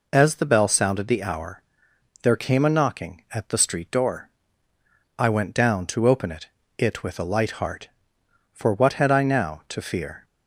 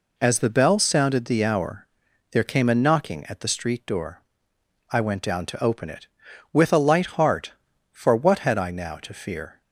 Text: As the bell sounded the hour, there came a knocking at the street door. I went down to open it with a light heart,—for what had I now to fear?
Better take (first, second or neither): second